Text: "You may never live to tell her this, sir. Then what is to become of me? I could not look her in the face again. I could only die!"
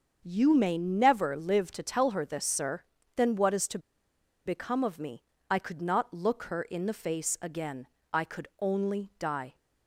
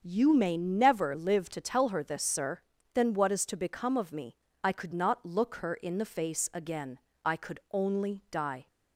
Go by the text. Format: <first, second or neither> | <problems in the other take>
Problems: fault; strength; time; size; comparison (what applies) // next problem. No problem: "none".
second | starts louder than the rest; until 1.2 s; 6.5 dB; also in the second // pauses between "to" and "become"; noticeable; at 3.7 s; 0.67 s long